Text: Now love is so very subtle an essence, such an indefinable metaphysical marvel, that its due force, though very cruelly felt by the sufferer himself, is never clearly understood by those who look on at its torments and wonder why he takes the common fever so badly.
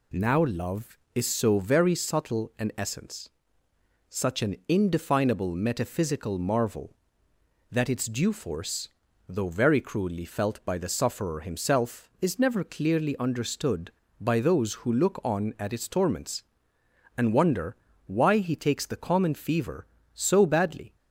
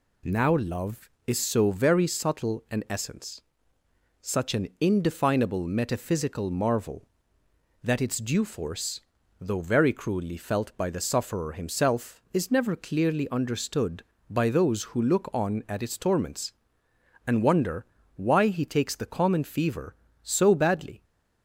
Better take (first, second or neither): neither